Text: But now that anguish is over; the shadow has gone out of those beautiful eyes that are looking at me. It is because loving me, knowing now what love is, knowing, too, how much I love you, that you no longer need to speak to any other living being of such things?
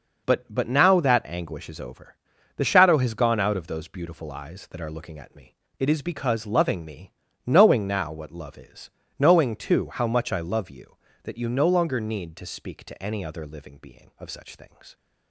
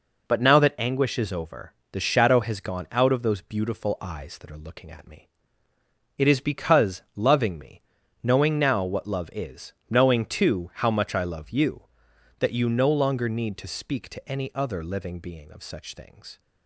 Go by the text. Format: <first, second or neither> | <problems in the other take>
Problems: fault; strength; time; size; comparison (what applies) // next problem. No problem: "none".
second | says "But" twice; at 0.4 s